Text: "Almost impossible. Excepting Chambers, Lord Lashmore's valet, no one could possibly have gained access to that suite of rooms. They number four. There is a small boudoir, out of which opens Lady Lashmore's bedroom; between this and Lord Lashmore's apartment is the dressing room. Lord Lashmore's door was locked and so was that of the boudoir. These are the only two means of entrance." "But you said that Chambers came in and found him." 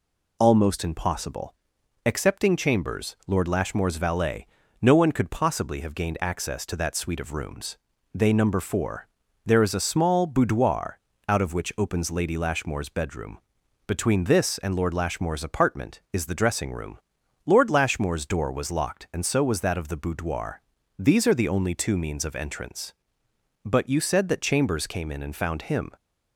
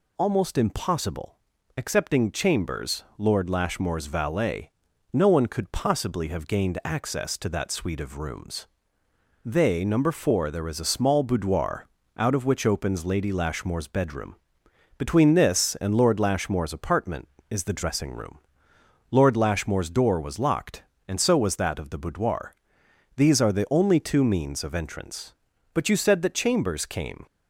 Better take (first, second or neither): first